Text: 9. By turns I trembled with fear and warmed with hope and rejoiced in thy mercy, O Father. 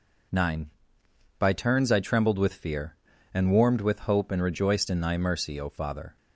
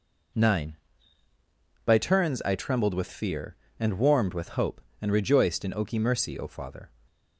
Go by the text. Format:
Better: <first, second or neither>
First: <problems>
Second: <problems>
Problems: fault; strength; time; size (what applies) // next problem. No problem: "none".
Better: first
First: none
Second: says "oki" for "thy"; at 5.7 s